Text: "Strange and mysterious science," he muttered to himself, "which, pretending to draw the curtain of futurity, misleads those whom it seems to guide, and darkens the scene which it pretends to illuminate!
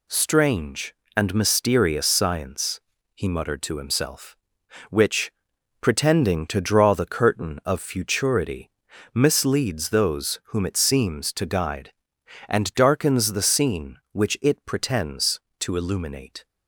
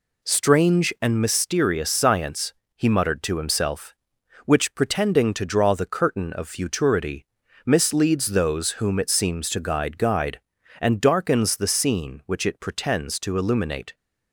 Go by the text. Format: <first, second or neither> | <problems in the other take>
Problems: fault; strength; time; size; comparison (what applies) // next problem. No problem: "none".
first | says "guide" twice; at 9.9 s